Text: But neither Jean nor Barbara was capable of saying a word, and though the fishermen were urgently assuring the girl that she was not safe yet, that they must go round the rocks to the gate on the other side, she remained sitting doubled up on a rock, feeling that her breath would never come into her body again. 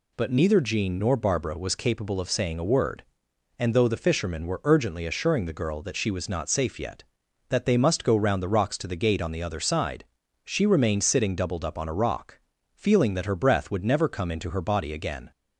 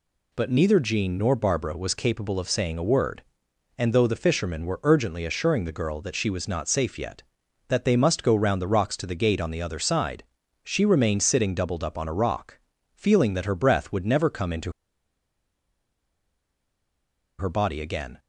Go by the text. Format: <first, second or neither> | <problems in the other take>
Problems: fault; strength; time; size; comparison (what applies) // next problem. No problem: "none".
first | pauses between "into" and "her"; strong; at 14.7 s; 2.6 s long